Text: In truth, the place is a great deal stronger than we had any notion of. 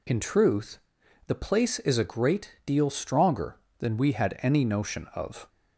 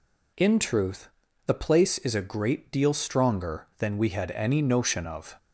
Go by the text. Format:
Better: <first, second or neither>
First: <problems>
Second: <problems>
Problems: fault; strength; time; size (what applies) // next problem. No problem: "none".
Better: neither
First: none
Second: none